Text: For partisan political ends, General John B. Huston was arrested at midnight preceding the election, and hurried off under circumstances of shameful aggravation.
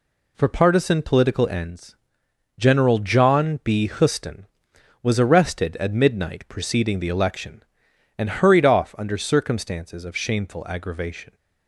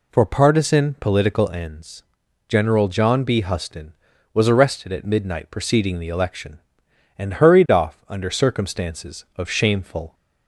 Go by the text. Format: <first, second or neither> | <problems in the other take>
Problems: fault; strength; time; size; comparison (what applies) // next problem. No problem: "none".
first | stops before "aggravation"; at 10.1 s